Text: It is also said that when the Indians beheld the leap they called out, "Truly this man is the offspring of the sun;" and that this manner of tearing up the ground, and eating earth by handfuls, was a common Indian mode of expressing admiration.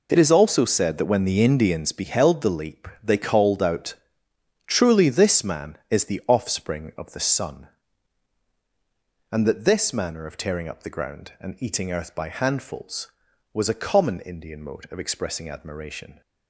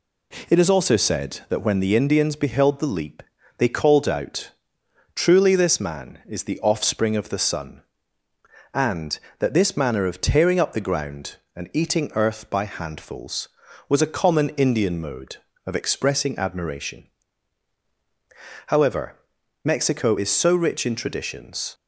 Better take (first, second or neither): first